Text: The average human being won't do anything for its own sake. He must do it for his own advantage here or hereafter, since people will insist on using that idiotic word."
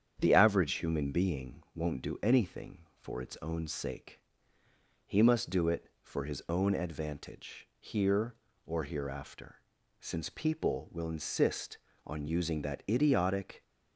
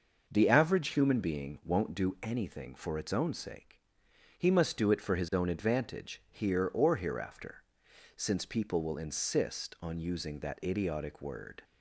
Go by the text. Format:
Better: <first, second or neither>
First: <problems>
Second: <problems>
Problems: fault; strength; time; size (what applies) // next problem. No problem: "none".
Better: second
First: starts louder than the rest; strong; until 1.1 s; 8.5 dB // stops before "word"; at 13.6 s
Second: starts louder than the rest; noticeable; until 1.2 s; 6 dB